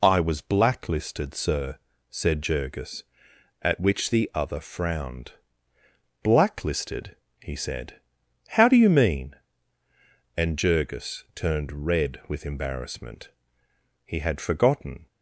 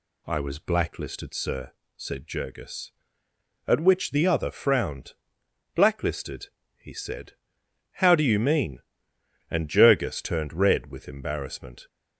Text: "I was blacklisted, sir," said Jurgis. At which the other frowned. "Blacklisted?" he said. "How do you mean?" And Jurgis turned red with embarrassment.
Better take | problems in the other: second | goes on to say "He had forgotten"; noticeable; from 14.0 s on; 1.0 s long

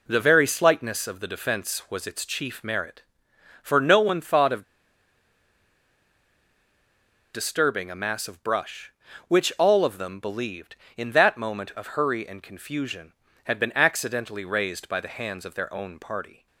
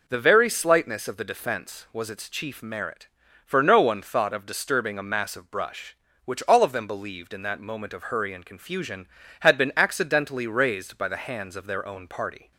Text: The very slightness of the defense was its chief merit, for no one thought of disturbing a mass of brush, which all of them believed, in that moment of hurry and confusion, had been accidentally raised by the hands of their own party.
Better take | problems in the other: second | pauses between "of" and "disturbing"; strong; at 4.6 s; 2.6 s long

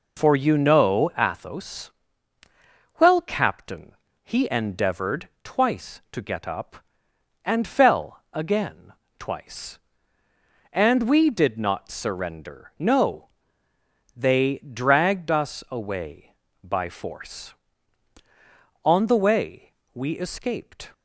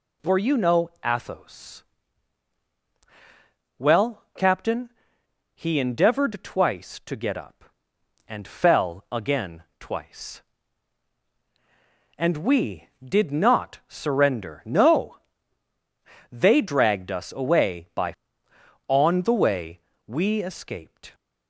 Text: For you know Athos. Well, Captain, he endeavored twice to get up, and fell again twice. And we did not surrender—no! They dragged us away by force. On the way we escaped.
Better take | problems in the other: first | pauses between "again" and "twice"; slight; at 9.6 s; 0.16 s long; slight in the first // skips "force"; at 18.5 s // pauses between "way" and "we"; slight; at 19.7 s; 0.28 s long; slight in the first

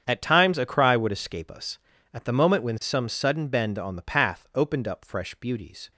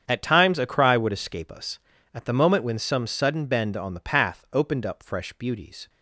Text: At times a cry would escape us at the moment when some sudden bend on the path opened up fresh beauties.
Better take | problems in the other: neither | starts louder than the rest; strong; the same in both

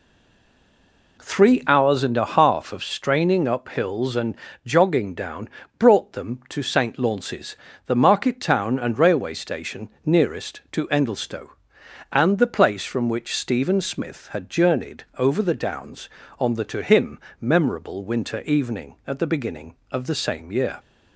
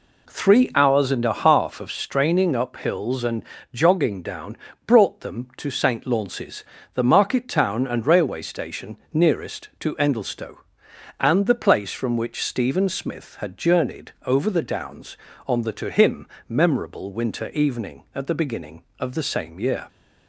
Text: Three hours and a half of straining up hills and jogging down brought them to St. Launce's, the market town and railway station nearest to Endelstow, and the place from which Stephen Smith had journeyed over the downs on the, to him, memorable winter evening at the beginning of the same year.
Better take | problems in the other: second | stays silent before the first word; noticeable; until 1.1 s; 1.1 s long // pauses between "and" and "jogging"; slight; at 4.3 s; 0.30 s long; slight in the second // pauses between "down" and "brought"; slight; at 5.4 s; 0.30 s long; slight in the second // pauses between "station" and "nearest"; slight; at 9.8 s; 0.16 s long; slight in the second

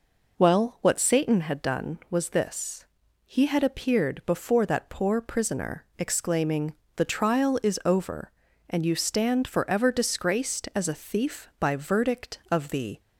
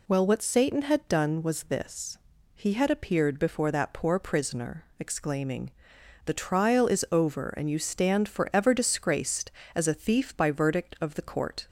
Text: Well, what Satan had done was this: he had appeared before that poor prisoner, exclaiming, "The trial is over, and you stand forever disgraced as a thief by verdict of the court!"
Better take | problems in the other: second | stops before "court"; at 12.9 s

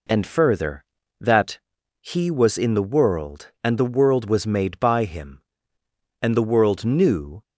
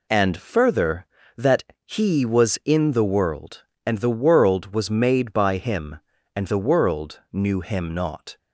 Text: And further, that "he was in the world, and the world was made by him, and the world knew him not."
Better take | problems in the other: second | pauses between "that" and "he"; at 1.5 s; 0.40 s long; slight in the second // stops before "him not"; at 7.4 s

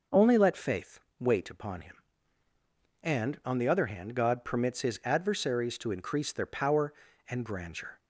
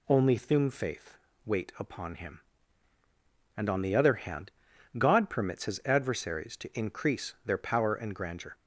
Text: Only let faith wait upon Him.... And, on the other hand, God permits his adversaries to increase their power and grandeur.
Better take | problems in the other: first | says "thum" for "let"; at 0.3 s // pauses between "faith" and "wait"; slight; at 1.1 s; 0.30 s long; slight in the first

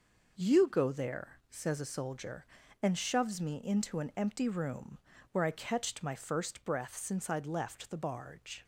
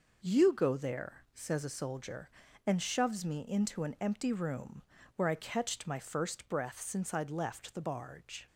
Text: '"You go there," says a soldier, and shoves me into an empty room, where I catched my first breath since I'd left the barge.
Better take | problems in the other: neither | none

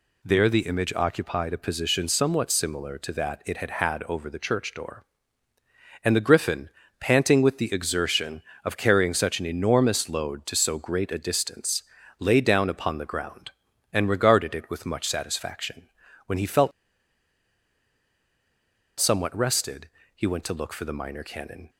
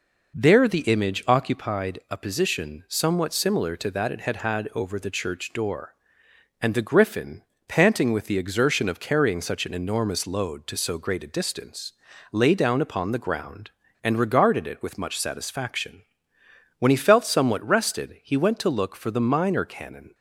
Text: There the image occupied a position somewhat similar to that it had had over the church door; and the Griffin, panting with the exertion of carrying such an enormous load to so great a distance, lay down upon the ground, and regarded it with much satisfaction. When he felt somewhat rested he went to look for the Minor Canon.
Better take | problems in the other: second | pauses between "felt" and "somewhat"; strong; at 16.7 s; 2.2 s long // pauses between "rested" and "he"; slight; at 19.8 s; 0.26 s long

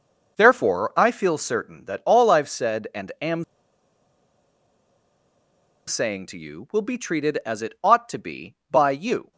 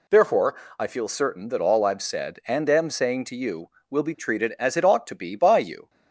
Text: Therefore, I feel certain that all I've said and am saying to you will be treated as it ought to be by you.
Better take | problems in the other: second | pauses between "am" and "saying"; strong; at 3.4 s; 2.4 s long

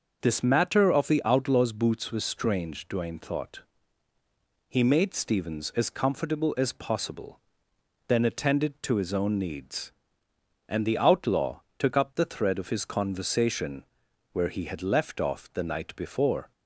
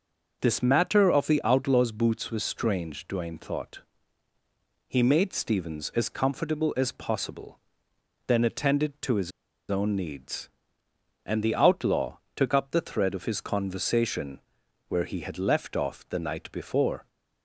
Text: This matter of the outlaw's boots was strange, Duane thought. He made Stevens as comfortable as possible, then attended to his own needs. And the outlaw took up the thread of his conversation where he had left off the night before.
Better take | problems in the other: first | pauses between "his" and "own"; at 9.3 s; 0.40 s long // pauses between "outlaw" and "took"; slight; at 12.1 s; 0.18 s long; slight in the first // pauses between "conversation" and "where"; noticeable; at 14.3 s; 0.48 s long; noticeable in the first

